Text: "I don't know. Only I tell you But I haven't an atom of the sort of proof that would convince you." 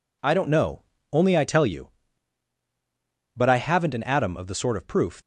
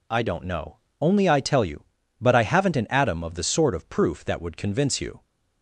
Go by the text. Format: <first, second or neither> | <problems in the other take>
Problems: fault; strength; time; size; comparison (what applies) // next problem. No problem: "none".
second | stops before "that would convince you"; at 5.2 s